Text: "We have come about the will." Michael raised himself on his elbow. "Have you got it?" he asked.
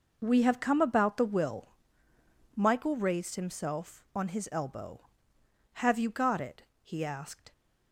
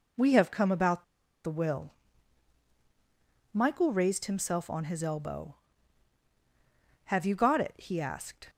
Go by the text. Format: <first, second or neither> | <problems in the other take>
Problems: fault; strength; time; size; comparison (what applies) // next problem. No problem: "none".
first | pauses between "about" and "the"; at 1.0 s; 0.40 s long